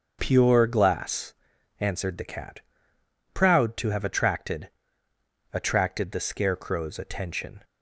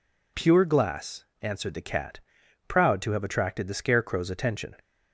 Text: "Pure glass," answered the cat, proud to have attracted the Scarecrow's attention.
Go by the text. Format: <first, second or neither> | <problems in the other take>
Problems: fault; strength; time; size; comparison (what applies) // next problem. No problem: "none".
second | starts louder than the rest; until 1.2 s; 6.5 dB // says "attracted" twice; at 5.5 s